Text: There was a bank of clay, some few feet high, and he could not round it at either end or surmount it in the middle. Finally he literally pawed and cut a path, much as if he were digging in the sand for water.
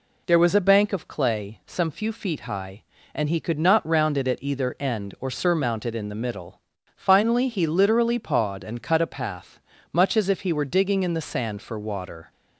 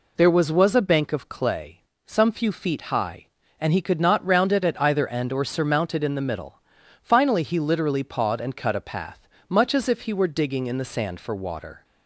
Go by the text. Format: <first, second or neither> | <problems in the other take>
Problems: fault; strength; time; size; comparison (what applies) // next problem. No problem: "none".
first | says "was" twice; at 0.4 s